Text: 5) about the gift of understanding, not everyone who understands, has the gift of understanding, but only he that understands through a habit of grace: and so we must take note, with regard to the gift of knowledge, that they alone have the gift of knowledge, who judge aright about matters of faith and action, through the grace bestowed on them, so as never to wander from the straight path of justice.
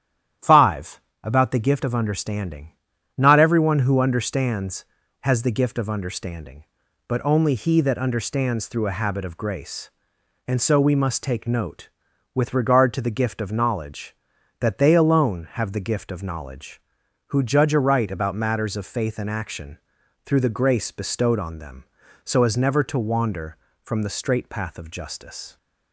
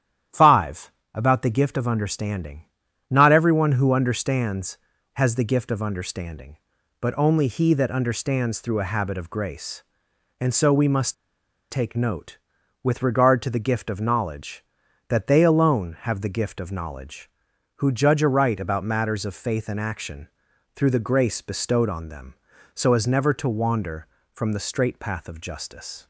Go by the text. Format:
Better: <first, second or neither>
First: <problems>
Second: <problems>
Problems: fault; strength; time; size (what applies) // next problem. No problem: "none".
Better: first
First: starts louder than the rest; strong; until 1.6 s; 10.5 dB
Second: starts louder than the rest; strong; until 1.5 s; 10.5 dB // pauses between "must" and "take"; noticeable; at 11.1 s; 0.58 s long